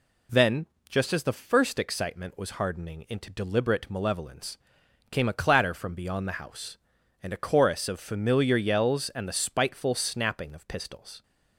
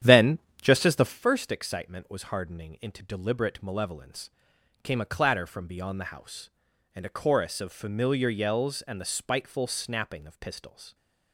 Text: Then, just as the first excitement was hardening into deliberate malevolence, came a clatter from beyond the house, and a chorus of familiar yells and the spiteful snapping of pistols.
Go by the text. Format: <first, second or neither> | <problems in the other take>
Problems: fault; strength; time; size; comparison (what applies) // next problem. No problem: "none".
first | starts louder than the rest; strong; until 1.3 s; 10 dB